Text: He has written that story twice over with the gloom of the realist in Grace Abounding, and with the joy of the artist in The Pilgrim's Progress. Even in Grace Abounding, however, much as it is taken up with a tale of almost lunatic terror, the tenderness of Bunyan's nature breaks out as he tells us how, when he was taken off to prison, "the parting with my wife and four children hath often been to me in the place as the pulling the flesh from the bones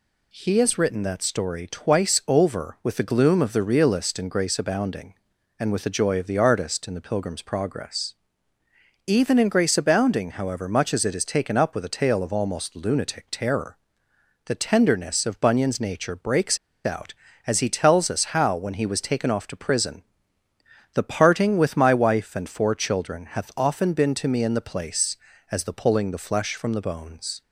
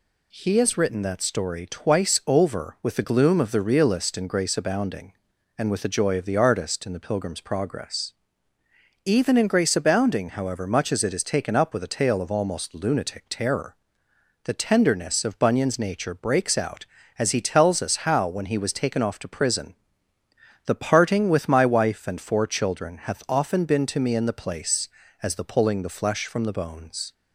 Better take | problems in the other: second | pauses between "breaks" and "out"; slight; at 16.5 s; 0.27 s long

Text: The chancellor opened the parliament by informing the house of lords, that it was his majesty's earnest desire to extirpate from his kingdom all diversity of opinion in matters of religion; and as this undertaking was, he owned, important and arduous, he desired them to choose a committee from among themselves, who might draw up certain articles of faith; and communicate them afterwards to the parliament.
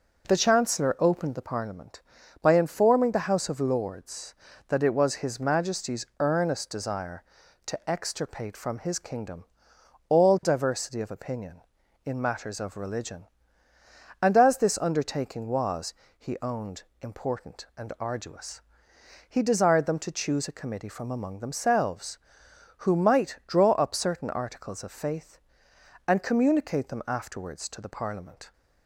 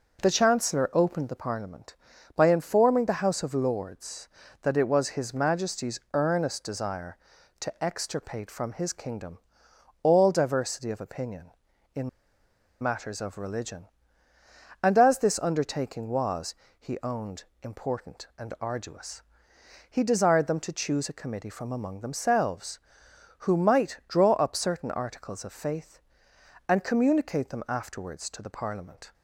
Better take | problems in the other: first | pauses between "kingdom" and "all"; noticeable; at 9.3 s; 0.64 s long; noticeable in the first // pauses between "in" and "matters"; noticeable; at 12.0 s; 0.73 s long

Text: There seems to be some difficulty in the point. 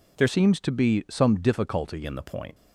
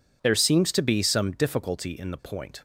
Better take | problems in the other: second | changes voice from "seems" to "difficulty"; from 0.2 to 2.0 s; 1.8 s long

